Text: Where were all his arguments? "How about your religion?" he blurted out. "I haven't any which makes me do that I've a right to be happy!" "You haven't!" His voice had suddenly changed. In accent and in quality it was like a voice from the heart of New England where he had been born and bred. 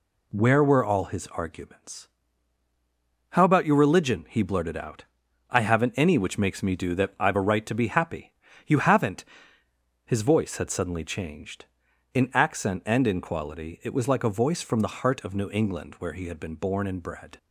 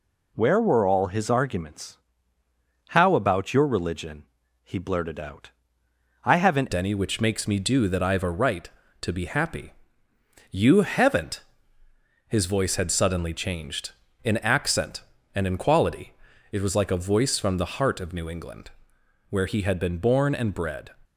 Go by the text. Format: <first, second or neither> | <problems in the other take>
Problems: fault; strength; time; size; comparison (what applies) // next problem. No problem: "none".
first | changes voice at "any"; from 6.7 s on; 14.2 s long // pauses between "quality" and "it"; at 16.1 s; 0.40 s long // pauses between "England" and "where"; noticeable; at 18.6 s; 0.60 s long